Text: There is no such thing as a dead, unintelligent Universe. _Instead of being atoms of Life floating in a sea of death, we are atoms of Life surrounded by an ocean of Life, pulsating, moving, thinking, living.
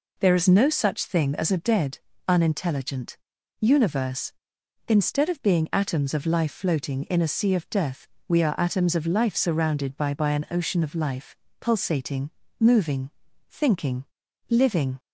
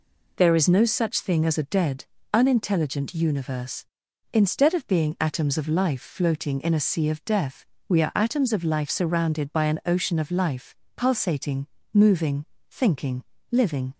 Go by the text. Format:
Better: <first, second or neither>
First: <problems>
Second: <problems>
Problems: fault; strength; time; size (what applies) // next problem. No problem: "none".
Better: second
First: pauses between "unintelligent" and "Universe"; at 3.1 s; 0.42 s long // says "by" twice; at 10.1 s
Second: none